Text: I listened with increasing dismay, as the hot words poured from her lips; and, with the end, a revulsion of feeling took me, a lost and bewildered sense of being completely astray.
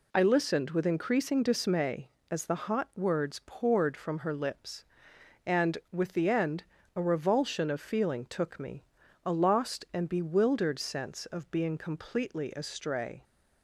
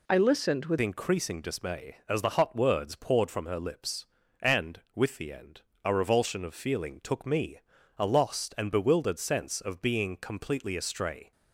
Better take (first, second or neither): first